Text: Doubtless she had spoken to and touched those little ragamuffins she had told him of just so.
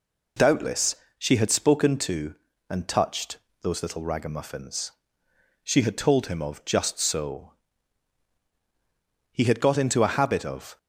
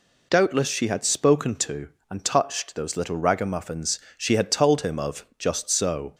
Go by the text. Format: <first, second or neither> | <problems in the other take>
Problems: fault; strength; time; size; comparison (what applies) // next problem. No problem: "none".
second | pauses between "Doubtless" and "she"; slight; at 0.9 s; 0.22 s long // pauses between "touched" and "those"; slight; at 3.3 s; 0.24 s long // pauses between "ragamuffins" and "she"; noticeable; at 4.9 s; 0.72 s long; slight in the second // goes on to say "He had got into a habit of"; from 9.3 s on; 1.4 s long